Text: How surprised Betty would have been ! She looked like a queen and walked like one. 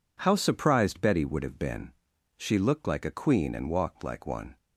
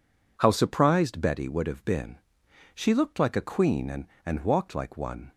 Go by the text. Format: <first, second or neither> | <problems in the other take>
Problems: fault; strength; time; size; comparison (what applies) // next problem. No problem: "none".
first | says "and" twice; at 4.2 s